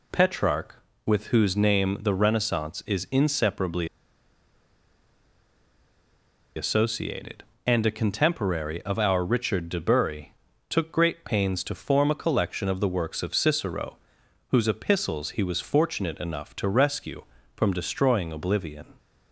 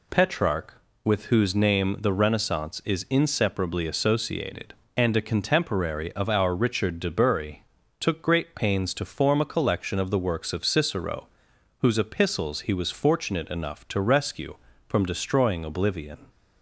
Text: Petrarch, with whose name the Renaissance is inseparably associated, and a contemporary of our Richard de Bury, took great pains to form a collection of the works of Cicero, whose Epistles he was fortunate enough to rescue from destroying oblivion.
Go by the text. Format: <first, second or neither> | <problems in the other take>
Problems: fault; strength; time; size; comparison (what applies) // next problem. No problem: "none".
second | pauses between "inseparably" and "associated"; strong; at 3.8 s; 2.6 s long